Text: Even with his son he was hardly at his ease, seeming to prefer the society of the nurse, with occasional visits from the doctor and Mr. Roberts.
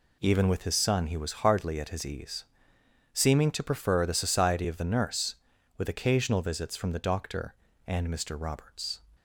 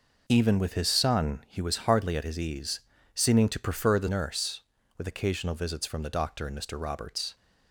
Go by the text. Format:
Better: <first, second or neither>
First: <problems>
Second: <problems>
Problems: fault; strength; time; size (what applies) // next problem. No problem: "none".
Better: first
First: none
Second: skips "society of the"; at 4.0 s